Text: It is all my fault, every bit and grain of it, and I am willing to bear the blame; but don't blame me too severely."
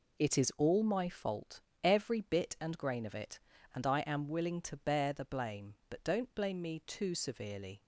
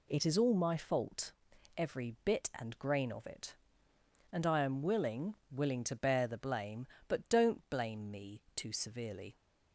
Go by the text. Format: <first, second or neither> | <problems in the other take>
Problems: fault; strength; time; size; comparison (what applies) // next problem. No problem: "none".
first | says "willing" twice; at 5.5 s